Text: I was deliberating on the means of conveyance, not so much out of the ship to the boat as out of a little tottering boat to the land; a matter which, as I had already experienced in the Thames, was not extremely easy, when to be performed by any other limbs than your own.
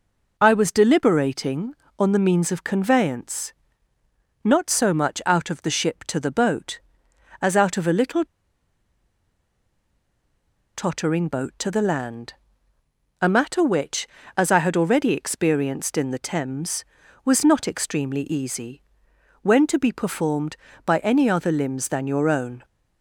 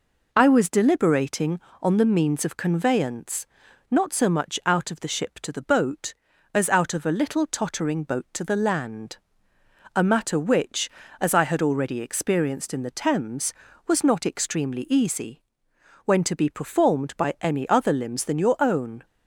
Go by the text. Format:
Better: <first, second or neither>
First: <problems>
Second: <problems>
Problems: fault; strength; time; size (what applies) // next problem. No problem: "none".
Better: second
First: pauses between "little" and "tottering"; strong; at 8.2 s; 2.4 s long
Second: none